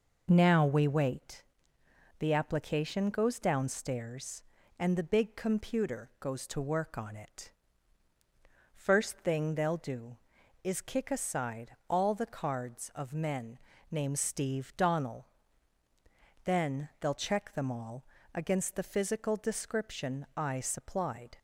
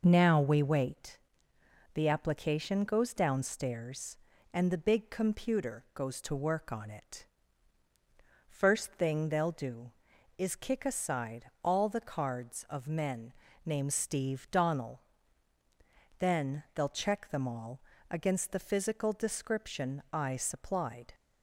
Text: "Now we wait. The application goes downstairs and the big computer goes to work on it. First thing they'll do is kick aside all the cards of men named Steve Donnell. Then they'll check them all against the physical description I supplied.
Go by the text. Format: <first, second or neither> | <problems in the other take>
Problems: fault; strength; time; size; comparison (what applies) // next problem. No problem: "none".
neither | pauses between "men" and "named"; slight; the same in both // pauses between "all" and "against"; slight; the same in both